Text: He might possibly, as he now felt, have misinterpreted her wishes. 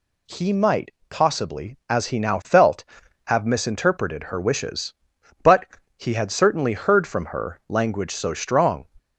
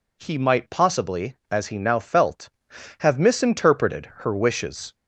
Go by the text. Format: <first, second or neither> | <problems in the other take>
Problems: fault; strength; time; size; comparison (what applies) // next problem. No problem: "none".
second | pauses between "might" and "possibly"; slight; at 0.8 s; 0.18 s long // goes on to say "But he had certainly heard from her language so strong"; strong; from 5.4 s on; 3.4 s long